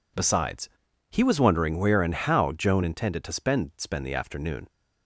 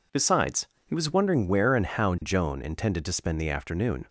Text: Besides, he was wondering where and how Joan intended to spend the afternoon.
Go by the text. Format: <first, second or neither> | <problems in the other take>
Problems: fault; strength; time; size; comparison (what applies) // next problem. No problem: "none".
second | says "spend" twice; at 3.7 s